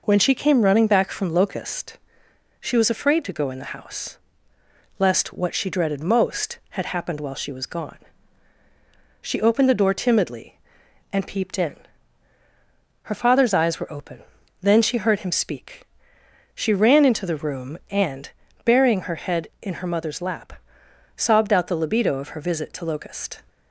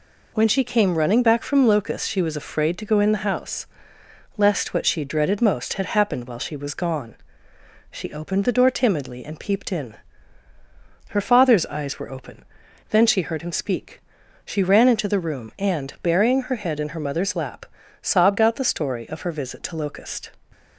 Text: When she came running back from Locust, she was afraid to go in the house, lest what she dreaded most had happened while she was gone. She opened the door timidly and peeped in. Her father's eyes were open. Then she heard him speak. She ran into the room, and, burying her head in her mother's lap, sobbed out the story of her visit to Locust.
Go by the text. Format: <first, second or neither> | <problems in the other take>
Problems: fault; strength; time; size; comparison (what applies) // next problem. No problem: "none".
second | says "libido" for "story"; at 21.7 s